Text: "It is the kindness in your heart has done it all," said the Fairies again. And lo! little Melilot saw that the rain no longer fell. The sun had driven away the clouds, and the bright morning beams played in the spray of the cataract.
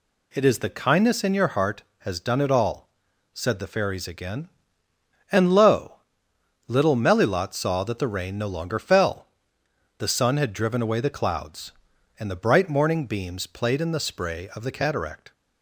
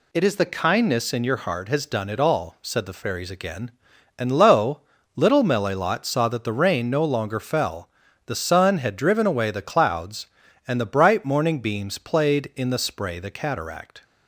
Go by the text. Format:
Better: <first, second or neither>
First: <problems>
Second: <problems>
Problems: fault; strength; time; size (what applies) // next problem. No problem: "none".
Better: first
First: none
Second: skips "of"; at 13.1 s